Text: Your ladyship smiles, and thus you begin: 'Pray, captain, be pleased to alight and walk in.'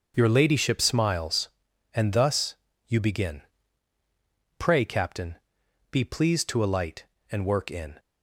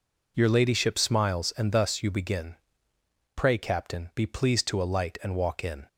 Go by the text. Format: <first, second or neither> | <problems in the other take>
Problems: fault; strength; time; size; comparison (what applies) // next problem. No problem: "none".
second | starts louder than the rest; until 1.1 s; 6.5 dB // pauses between "thus" and "you"; slight; at 2.5 s; 0.32 s long // says "work" for "walk"; at 7.4 s